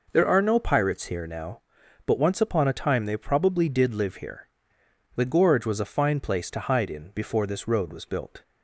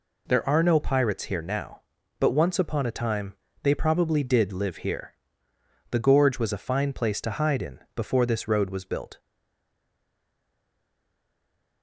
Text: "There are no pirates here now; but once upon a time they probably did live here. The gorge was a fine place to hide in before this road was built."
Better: first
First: none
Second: pauses between "time" and "they"; slight; at 3.3 s; 0.26 s long // pauses between "in" and "before"; slight; at 7.7 s; 0.16 s long // stays silent after the last word; strong; from 9.1 s on; 2.7 s long

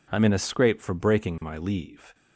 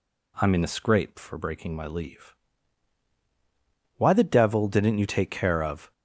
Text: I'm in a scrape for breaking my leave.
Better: first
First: none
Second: goes on to say "Why the devil didn't you take care of"; strong; from 3.9 s on; 1.9 s long

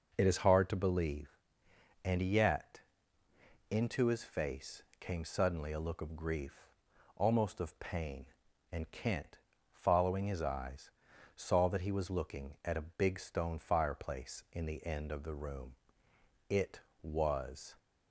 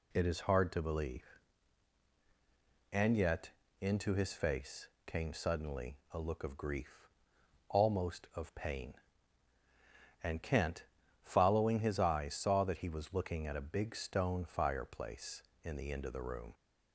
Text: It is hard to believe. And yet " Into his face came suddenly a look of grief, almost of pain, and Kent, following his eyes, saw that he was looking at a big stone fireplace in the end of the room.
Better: second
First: pauses between "face" and "came"; slight; at 4.8 s; 0.16 s long // goes on to say "It was"; noticeable; from 16.4 s on; 1.2 s long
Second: pauses between "face" and "came"; slight; at 4.8 s; 0.22 s long

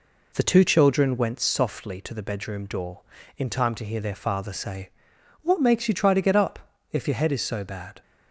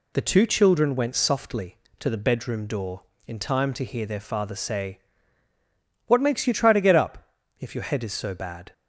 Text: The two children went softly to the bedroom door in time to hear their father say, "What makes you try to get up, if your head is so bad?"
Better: neither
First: none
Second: none

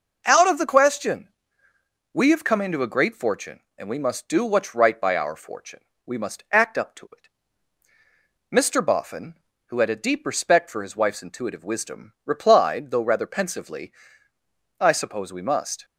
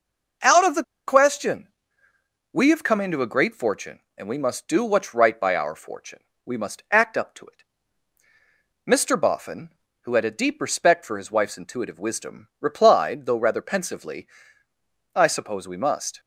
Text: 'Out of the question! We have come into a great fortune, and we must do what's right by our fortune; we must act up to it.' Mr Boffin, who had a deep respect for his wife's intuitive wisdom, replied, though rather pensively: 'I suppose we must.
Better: first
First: none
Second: pauses between "the" and "question"; slight; at 0.8 s; 0.24 s long

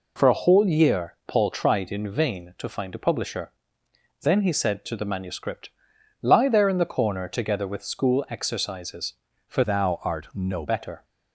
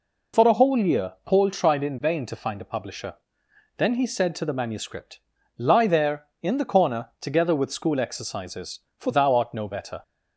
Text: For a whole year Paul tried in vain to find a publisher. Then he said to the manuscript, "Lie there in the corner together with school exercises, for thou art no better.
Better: second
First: changes voice from "thou" to "no"; from 9.6 to 10.6 s; 1.0 s long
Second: none

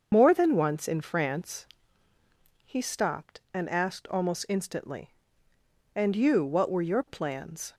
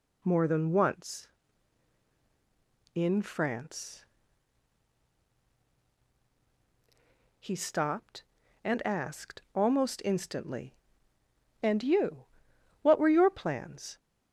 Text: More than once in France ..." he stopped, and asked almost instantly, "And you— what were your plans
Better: second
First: loses the start of "More"; at 0.1 s; 55 ms // starts louder than the rest; until 1.1 s; 6.5 dB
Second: none

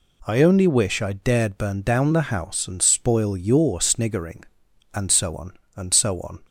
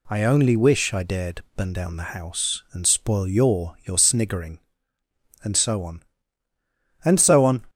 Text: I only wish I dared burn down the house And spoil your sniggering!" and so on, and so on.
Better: first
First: none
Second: says "your" twice; at 3.8 s

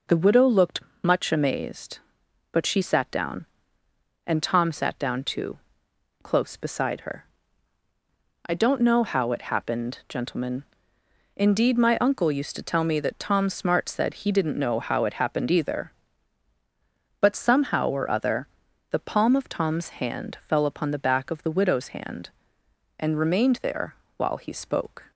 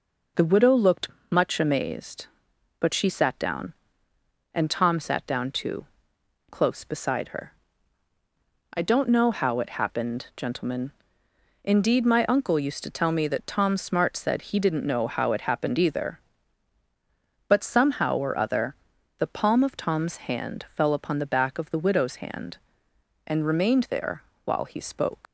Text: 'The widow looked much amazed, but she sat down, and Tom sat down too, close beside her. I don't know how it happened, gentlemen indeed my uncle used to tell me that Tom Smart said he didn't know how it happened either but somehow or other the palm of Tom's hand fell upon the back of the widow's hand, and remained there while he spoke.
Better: first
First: pauses between "looked" and "much"; slight; at 0.8 s; 0.22 s long // pauses between "gentlemen" and "indeed"; noticeable; at 10.6 s; 0.76 s long // pauses between "other" and "the"; at 18.4 s; 0.42 s long // pauses between "there" and "while"; slight; at 23.9 s; 0.24 s long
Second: pauses between "looked" and "much"; slight; at 1.0 s; 0.22 s long // pauses between "gentlemen" and "indeed"; noticeable; at 10.9 s; 0.76 s long // pauses between "other" and "the"; at 18.7 s; 0.42 s long // pauses between "there" and "while"; slight; at 24.2 s; 0.24 s long // leaves "spoke" unfinished; at 25.2 s; 135 ms

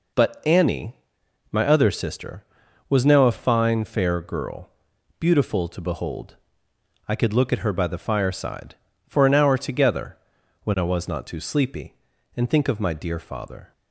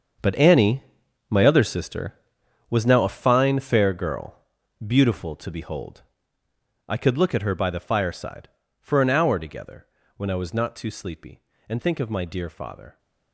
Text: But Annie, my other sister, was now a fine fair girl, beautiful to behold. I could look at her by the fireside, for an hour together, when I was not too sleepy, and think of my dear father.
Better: first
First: none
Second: gets quieter; strong; throughout; 13.5 dB

